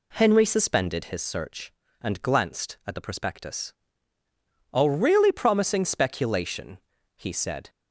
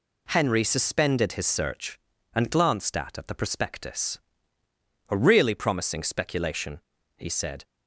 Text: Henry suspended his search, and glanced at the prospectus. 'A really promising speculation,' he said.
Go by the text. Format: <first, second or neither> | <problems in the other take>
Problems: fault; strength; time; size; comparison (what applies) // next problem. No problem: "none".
first | says "at" twice; at 3.1 s